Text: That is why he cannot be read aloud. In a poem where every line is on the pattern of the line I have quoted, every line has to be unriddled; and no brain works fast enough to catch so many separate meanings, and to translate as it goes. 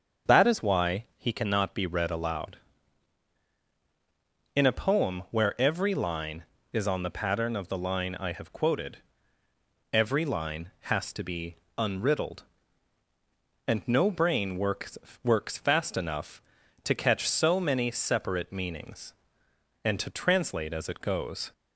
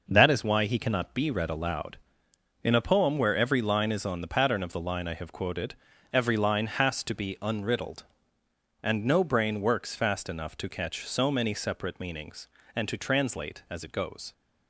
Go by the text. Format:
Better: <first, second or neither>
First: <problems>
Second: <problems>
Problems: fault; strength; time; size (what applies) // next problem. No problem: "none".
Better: second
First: starts louder than the rest; until 1.4 s; 6.5 dB // pauses between "be" and "unriddled"; slight; at 11.5 s; 0.20 s long // says "works" twice; at 15.2 s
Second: none